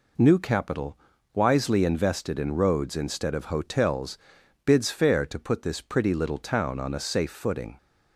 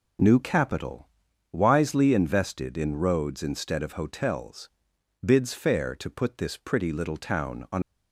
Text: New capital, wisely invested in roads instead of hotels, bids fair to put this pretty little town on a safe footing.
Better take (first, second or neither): first